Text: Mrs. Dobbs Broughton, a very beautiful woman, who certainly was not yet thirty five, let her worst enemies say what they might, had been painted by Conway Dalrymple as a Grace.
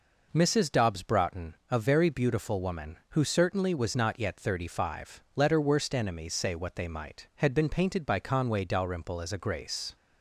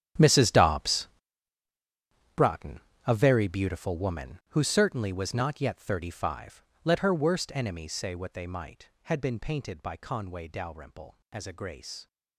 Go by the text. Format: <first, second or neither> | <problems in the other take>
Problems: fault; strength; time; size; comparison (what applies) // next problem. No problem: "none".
first | gets quieter; strong; throughout; 16.5 dB // pauses between "Dobbs" and "Broughton"; strong; at 1.0 s; 1.2 s long